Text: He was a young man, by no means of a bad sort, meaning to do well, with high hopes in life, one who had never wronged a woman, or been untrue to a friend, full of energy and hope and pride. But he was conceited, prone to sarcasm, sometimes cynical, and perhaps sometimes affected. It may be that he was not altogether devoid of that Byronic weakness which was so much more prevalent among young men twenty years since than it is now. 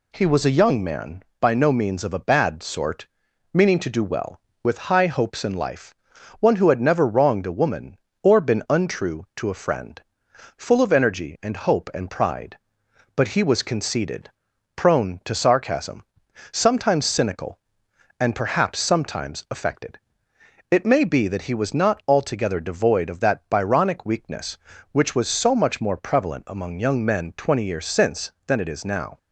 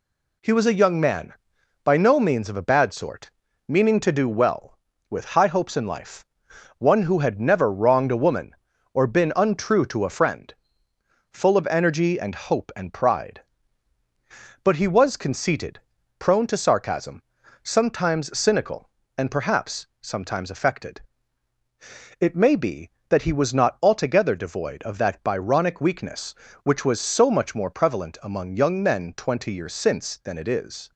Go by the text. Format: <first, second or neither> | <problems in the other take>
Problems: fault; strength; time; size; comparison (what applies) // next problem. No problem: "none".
first | pauses between "perhaps" and "sometimes"; slight; at 19.8 s; 0.16 s long // stops before "now"; at 30.9 s